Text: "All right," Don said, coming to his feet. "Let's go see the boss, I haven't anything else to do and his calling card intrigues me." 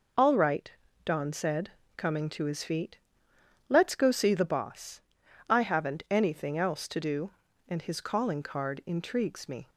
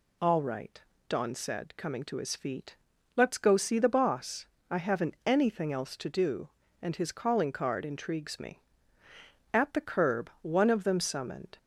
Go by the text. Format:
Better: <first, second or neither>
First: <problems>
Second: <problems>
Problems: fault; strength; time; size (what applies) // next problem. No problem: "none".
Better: first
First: none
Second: goes on to say "At the curb one of them summoned"; strong; from 9.5 s on; 2.0 s long